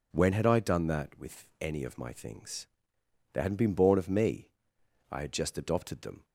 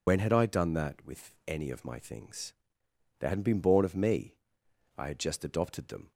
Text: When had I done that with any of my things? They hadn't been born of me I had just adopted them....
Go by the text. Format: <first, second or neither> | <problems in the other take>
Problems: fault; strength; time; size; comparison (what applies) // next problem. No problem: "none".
first | loses the start of "When"; at 0.0 s; 80 ms // pauses between "me" and "I"; noticeable; at 4.3 s; 0.60 s long; noticeable in the first